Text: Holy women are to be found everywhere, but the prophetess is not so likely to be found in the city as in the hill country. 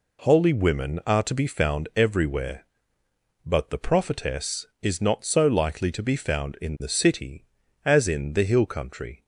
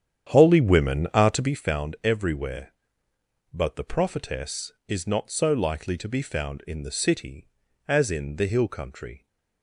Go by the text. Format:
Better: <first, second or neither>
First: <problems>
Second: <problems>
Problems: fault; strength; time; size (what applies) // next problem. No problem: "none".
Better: first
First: none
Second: starts louder than the rest; strong; until 1.6 s; 9 dB